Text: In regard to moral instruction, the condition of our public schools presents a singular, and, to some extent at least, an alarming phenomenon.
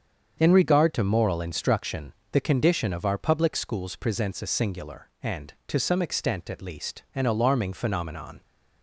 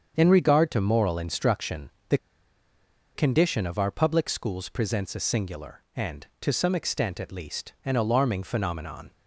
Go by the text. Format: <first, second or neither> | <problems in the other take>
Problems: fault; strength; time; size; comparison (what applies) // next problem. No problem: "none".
first | starts louder than the rest; until 1.1 s; 7 dB; also in the first // pauses between "the" and "condition"; noticeable; at 2.1 s; 0.97 s long